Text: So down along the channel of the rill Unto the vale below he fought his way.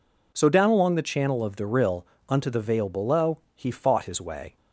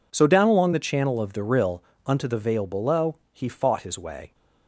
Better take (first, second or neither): first